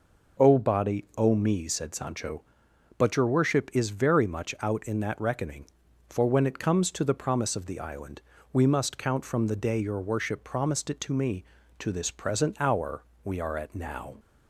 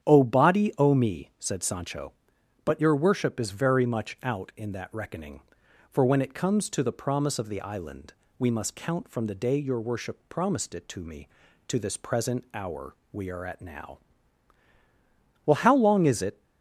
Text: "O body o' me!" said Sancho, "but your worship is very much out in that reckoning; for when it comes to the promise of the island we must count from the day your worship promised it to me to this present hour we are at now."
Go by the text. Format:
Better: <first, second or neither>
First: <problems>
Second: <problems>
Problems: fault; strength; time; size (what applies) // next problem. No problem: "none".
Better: first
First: pauses between "island" and "we"; slight; at 8.2 s; 0.28 s long // pauses between "hour" and "we"; slight; at 13.0 s; 0.20 s long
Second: starts louder than the rest; strong; until 1.1 s; 9 dB // pauses between "island" and "we"; slight; at 8.1 s; 0.28 s long // pauses between "hour" and "we"; slight; at 12.9 s; 0.16 s long // goes on to say "Well how long is it"; noticeable; from 15.4 s on; 0.96 s long